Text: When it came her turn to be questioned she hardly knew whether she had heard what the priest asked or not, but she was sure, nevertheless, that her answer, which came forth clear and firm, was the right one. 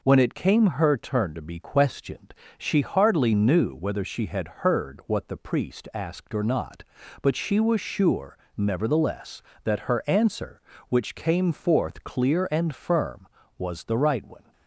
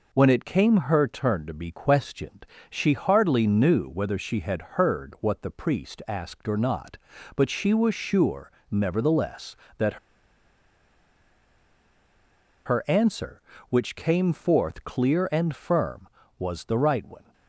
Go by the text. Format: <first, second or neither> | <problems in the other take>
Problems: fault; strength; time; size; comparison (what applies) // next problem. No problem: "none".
first | pauses between "questioned" and "she"; slight; at 2.4 s; 0.24 s long; slight in the first // pauses between "had" and "heard"; slight; at 4.5 s; 0.16 s long; slight in the first // pauses between "that" and "her"; strong; at 9.9 s; 2.6 s long